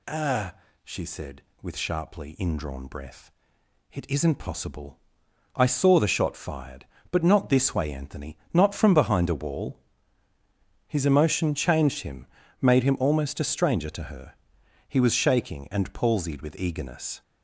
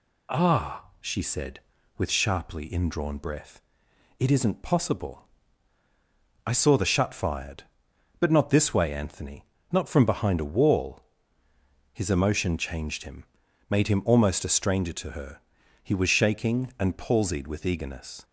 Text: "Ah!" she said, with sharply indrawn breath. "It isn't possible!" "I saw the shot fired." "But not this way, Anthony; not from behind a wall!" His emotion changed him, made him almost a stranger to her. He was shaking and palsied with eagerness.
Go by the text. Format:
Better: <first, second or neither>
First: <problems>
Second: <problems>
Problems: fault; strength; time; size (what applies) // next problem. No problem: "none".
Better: first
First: none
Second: says "shut" for "shot"; at 6.8 s